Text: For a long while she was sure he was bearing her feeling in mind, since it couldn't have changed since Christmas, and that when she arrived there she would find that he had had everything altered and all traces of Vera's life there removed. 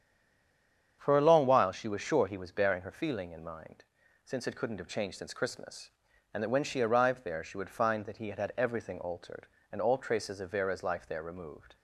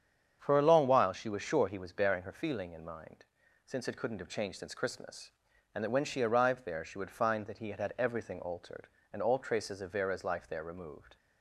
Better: second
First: stays silent before the first word; until 0.9 s; 0.9 s long // starts louder than the rest; strong; until 2.0 s; 8 dB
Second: starts louder than the rest; strong; until 1.4 s; 8 dB

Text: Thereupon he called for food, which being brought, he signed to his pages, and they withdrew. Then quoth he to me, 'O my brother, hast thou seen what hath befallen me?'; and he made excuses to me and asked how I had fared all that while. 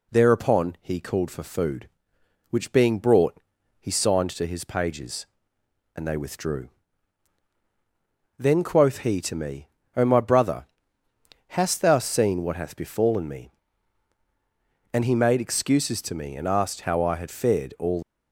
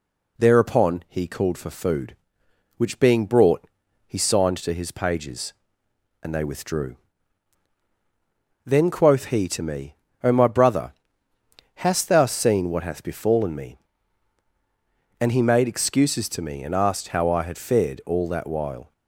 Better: second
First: stops before "that while"; at 18.0 s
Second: none

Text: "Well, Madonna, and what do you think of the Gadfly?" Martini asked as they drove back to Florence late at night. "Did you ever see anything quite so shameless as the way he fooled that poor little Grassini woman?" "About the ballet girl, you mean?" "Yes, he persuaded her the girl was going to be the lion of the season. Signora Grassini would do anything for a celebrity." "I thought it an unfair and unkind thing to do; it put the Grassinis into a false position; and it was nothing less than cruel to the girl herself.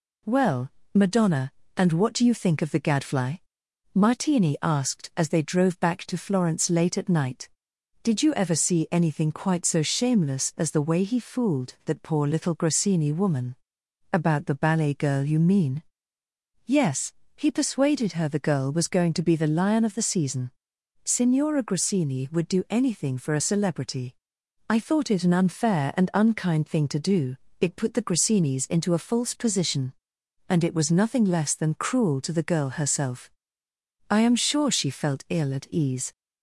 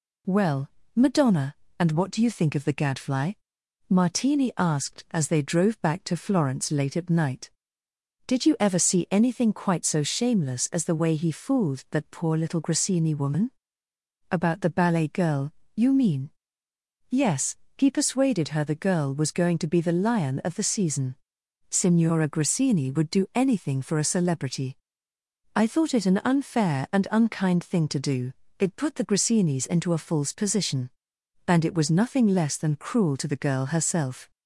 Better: second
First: goes on to say "I am sure she felt ill at ease"; strong; from 34.0 s on; 2.0 s long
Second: none

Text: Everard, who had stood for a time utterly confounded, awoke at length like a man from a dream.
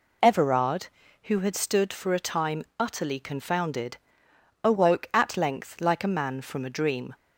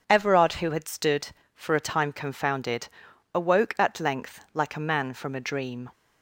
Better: first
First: none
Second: skips "utterly"; at 2.1 s

